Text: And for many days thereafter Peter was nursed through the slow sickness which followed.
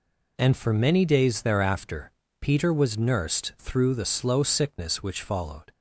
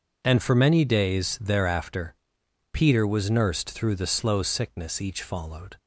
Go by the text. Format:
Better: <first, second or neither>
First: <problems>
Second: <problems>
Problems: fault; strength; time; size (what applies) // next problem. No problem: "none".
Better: first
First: pauses between "thereafter" and "Peter"; slight; at 2.1 s; 0.30 s long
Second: pauses between "thereafter" and "Peter"; noticeable; at 2.1 s; 0.58 s long // says "each" for "which"; at 5.0 s